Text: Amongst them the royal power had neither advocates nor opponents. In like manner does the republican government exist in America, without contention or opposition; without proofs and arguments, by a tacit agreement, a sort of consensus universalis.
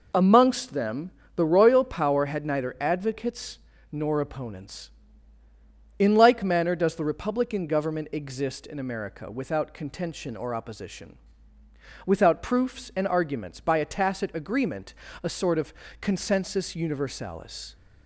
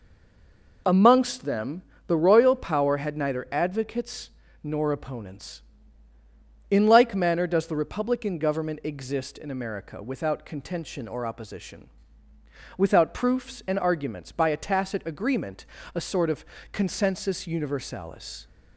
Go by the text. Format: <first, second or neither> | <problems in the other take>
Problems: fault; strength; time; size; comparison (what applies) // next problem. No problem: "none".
first | stays silent before the first word; slight; until 0.8 s; 0.8 s long // pauses between "them" and "the"; slight; at 1.8 s; 0.24 s long; slight in the first // pauses between "advocates" and "nor"; slight; at 4.2 s; 0.32 s long; slight in the first // pauses between "of" and "consensus"; slight; at 16.4 s; 0.28 s long; slight in the first